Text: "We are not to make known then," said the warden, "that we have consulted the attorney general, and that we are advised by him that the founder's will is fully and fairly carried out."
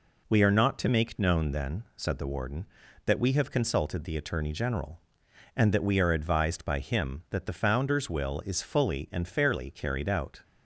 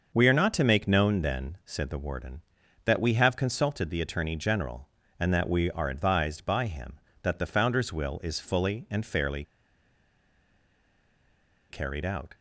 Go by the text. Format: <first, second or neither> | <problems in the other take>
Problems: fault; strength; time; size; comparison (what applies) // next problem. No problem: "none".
first | starts louder than the rest; until 1.1 s; 6 dB // pauses between "fairly" and "carried"; strong; at 9.4 s; 2.2 s long